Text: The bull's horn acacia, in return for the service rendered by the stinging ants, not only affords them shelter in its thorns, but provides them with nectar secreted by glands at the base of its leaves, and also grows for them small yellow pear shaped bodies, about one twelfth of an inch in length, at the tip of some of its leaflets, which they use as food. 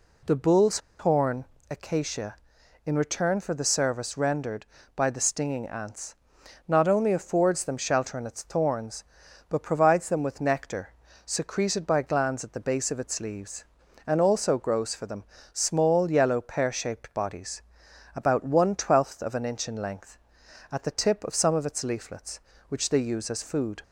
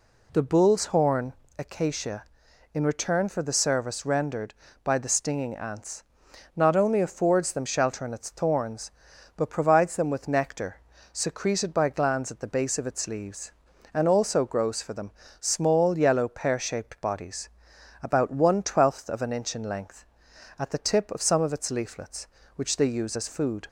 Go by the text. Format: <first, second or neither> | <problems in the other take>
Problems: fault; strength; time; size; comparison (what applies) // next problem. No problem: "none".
second | pauses between "bull's" and "horn"; slight; at 0.7 s; 0.21 s long // pauses between "horn" and "acacia"; slight; at 1.4 s; 0.26 s long; slight in the second // pauses between "nectar" and "secreted"; slight; at 10.9 s; 0.30 s long; slight in the second // pauses between "them" and "small"; slight; at 15.2 s; 0.30 s long; slight in the second